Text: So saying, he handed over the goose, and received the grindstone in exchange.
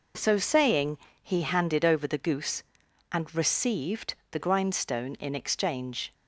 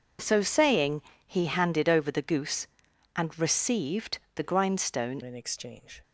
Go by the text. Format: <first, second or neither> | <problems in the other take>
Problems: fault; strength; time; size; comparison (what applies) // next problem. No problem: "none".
first | pauses between "received" and "the"; slight; at 4.1 s; 0.16 s long; slight in the first // changes voice at "in"; from 5.2 s on; 0.8 s long